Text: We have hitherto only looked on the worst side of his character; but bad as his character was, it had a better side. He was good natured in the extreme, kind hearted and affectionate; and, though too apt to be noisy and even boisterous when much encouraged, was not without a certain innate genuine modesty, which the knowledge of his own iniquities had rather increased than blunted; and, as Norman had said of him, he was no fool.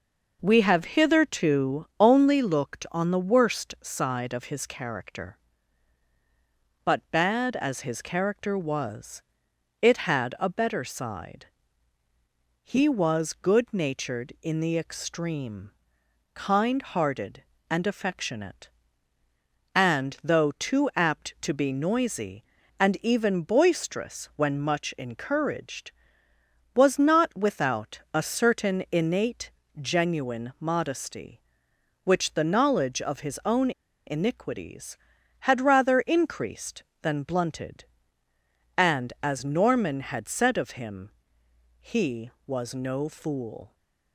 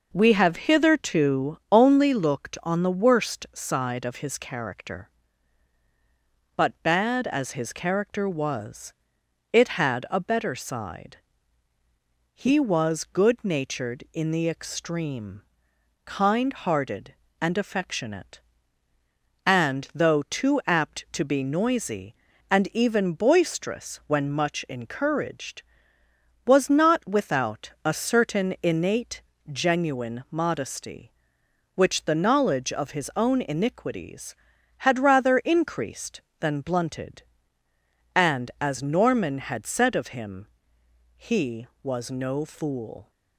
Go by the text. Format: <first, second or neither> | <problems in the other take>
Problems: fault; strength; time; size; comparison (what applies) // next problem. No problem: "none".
second | pauses between "innate" and "genuine"; slight; at 29.5 s; 0.30 s long; slight in the second // pauses between "own" and "iniquities"; slight; at 33.7 s; 0.36 s long